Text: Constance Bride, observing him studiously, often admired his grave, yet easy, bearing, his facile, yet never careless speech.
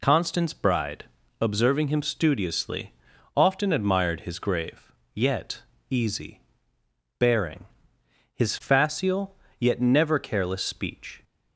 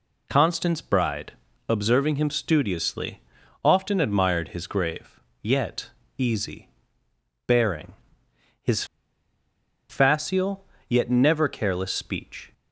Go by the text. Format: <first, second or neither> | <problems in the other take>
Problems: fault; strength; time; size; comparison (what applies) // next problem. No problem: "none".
first | pauses between "yet" and "easy"; slight; at 5.9 s; 0.28 s long; slight in the first // pauses between "his" and "facile"; at 8.8 s; 1.0 s long